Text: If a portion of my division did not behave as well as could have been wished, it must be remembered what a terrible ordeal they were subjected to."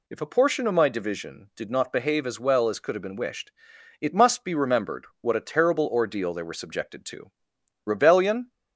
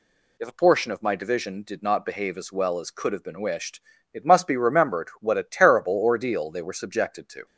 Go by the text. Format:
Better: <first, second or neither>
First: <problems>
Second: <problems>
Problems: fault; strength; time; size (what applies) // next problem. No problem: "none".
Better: second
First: goes on to say "Rebellion"; noticeable; from 7.8 s on; 0.68 s long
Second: none